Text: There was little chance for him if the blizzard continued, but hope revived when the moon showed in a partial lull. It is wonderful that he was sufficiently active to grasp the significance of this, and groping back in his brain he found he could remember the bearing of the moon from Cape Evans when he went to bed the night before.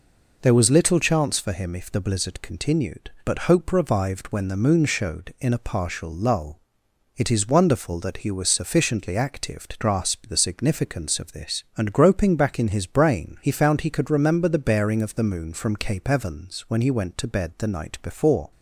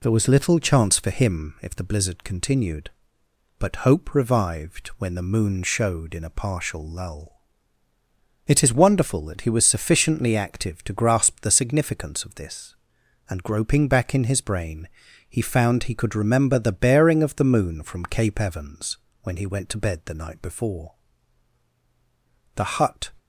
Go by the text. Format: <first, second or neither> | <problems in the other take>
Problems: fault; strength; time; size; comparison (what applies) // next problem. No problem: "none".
first | pauses between "brain" and "he"; at 14.8 s; 0.42 s long // pauses between "Evans" and "when"; slight; at 18.9 s; 0.24 s long // goes on to say "The hut"; from 22.5 s on; 0.56 s long